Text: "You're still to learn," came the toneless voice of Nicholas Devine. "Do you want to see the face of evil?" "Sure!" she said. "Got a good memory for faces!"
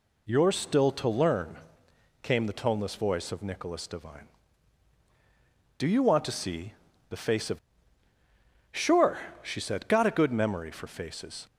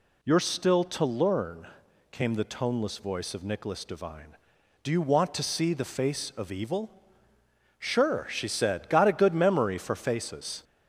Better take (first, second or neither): second